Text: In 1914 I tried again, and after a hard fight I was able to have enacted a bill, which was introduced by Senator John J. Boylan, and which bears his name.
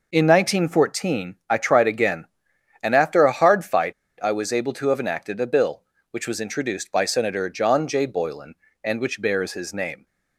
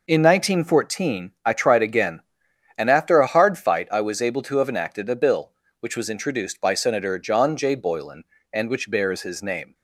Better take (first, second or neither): second